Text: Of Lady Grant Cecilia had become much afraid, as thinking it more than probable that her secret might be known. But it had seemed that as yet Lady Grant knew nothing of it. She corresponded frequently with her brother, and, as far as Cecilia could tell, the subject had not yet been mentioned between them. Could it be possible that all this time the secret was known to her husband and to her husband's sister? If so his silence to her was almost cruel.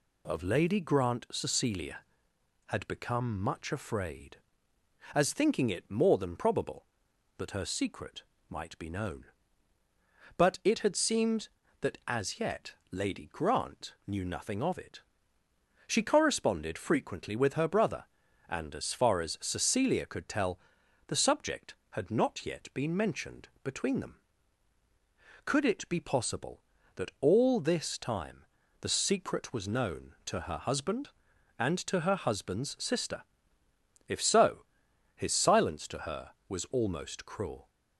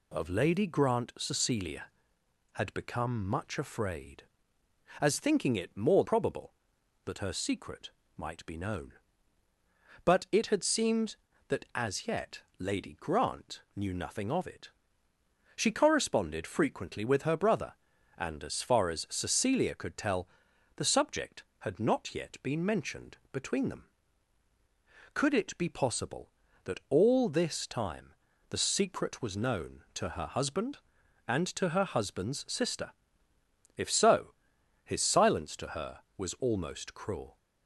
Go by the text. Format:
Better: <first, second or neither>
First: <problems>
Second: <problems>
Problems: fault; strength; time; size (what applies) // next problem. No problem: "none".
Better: first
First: pauses between "secret" and "might"; slight; at 8.2 s; 0.26 s long // pauses between "yet" and "Lady"; slight; at 12.7 s; 0.18 s long // pauses between "time" and "the"; at 28.3 s; 0.42 s long // pauses between "so" and "his"; noticeable; at 34.5 s; 0.56 s long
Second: skips "than"; at 6.0 s // pauses between "secret" and "might"; slight; at 7.9 s; 0.26 s long // pauses between "yet" and "Lady"; slight; at 12.3 s; 0.18 s long // pauses between "time" and "the"; at 28.0 s; 0.42 s long // pauses between "so" and "his"; noticeable; at 34.2 s; 0.56 s long